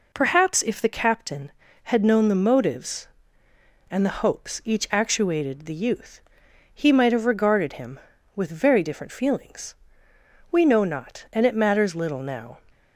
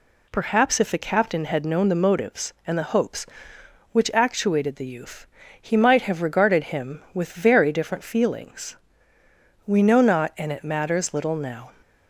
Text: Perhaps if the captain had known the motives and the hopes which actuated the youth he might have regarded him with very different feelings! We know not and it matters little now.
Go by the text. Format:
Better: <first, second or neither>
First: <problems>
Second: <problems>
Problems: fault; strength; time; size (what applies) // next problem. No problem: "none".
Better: second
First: says "each" for "which"; at 4.6 s // pauses between "youth" and "he"; noticeable; at 6.1 s; 0.54 s long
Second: pauses between "youth" and "he"; slight; at 5.2 s; 0.34 s long